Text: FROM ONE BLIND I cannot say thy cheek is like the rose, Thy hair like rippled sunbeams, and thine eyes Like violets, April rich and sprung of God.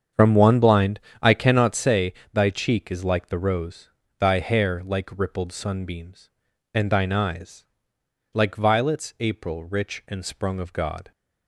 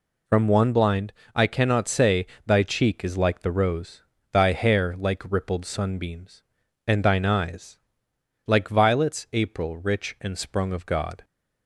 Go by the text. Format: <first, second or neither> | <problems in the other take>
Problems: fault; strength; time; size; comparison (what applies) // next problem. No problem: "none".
second | starts louder than the rest; strong; until 1.8 s; 7.5 dB // pauses between "BLIND" and "I"; slight; at 0.9 s; 0.22 s long; slight in the second // pauses between "say" and "thy"; slight; at 2.1 s; 0.20 s long; slight in the second // pauses between "eyes" and "Like"; noticeable; at 7.6 s; 0.68 s long; noticeable in the second